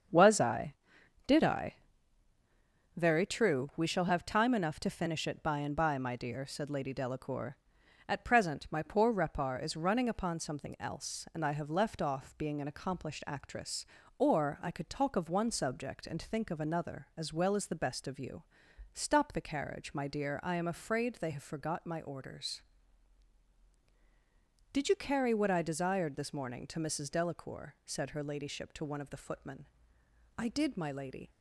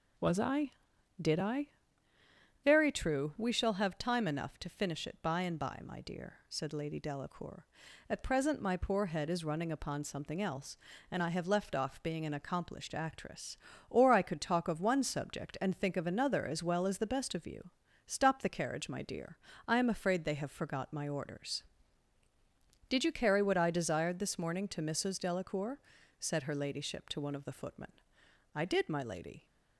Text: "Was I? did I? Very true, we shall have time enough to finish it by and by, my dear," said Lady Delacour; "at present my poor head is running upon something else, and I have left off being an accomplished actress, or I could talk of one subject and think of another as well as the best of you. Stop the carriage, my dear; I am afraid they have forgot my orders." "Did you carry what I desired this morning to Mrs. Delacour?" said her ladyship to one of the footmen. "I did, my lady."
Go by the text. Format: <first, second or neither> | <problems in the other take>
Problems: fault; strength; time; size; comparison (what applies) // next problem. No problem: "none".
second | starts louder than the rest; strong; until 1.6 s; 7 dB // says "repar" for "head"; at 9.1 s